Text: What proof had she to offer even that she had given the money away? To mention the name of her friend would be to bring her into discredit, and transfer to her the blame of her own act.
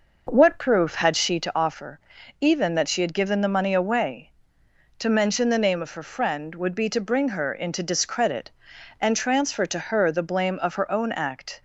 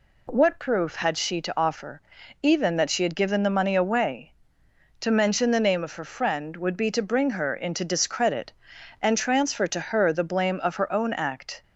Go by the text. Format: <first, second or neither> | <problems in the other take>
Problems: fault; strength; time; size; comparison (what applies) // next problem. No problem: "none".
second | starts louder than the rest; noticeable; until 1.6 s; 5.5 dB // pauses between "offer" and "even"; at 2.0 s; 0.40 s long; also in the second